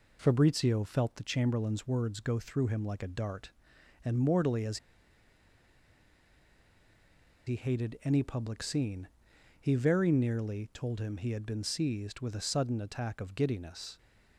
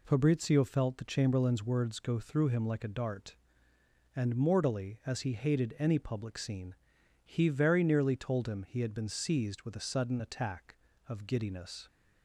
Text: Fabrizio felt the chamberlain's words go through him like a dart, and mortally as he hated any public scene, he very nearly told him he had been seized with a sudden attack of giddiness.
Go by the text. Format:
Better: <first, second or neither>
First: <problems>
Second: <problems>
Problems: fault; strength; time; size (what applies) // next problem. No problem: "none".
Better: second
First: pauses between "as" and "he"; strong; at 4.7 s; 2.7 s long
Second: none